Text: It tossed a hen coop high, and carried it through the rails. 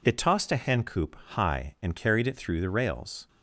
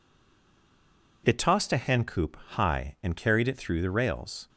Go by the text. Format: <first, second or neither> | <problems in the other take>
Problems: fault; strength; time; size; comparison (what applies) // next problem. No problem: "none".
first | stays silent before the first word; noticeable; until 1.2 s; 1.2 s long